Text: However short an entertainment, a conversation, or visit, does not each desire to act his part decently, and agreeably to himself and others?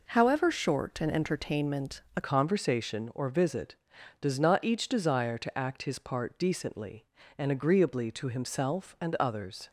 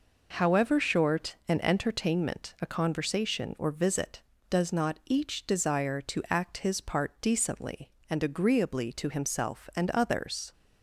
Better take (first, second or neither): second